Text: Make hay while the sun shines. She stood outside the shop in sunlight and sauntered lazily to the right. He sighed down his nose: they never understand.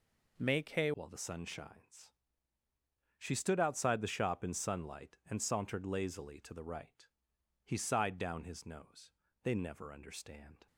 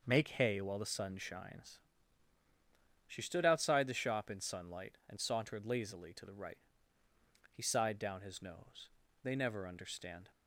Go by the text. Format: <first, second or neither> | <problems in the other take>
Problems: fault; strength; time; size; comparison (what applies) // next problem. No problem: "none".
second | changes voice at "while"; from 0.9 s on; 9.7 s long